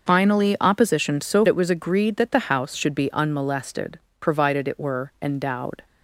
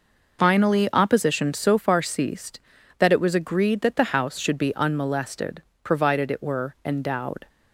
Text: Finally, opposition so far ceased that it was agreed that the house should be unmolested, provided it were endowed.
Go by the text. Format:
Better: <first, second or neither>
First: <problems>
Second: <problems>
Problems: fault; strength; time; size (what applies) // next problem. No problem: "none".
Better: second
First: starts louder than the rest; until 1.1 s; 6.5 dB // skips "far ceased that"; at 1.4 s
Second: none